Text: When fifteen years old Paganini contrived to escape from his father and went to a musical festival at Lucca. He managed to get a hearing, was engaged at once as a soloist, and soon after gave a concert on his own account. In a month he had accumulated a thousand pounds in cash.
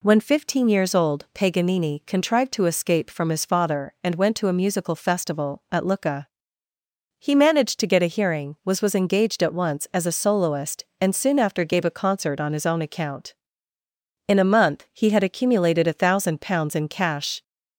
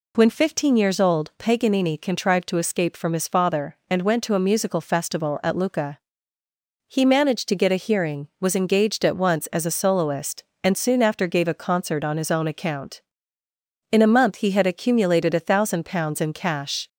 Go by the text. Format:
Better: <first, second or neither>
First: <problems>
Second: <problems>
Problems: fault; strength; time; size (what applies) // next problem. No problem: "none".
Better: second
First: says "was" twice; at 8.8 s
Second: none